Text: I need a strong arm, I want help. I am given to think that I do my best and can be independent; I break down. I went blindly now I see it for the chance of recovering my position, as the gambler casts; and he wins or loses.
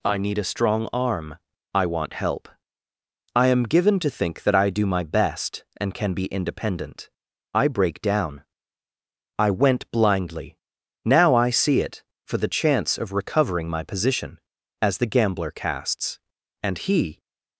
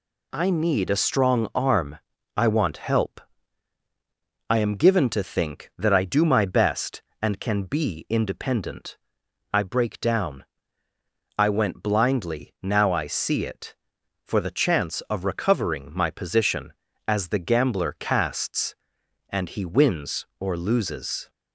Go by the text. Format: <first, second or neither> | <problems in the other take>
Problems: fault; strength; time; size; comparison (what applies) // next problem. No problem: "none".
second | pauses between "blindly" and "now"; noticeable; at 10.5 s; 0.48 s long // stops before "wins or loses"; at 17.1 s